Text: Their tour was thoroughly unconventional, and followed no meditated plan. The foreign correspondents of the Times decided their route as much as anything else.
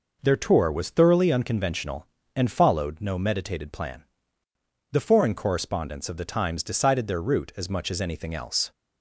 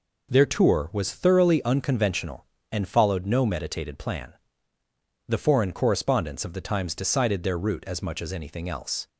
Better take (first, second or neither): neither